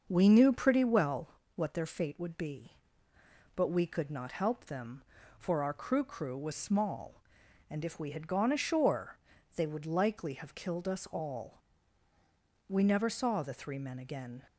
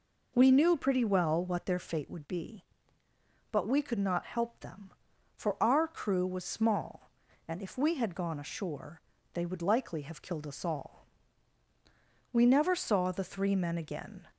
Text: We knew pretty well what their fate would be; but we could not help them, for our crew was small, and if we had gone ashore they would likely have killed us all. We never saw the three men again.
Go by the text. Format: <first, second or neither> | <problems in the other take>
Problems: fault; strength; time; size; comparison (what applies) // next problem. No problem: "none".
second | starts louder than the rest; until 1.0 s; 6 dB // pauses between "well" and "what"; slight; at 1.2 s; 0.30 s long // says "crew" twice; at 6.0 s // pauses between "ashore" and "they"; at 9.1 s; 0.40 s long; slight in the second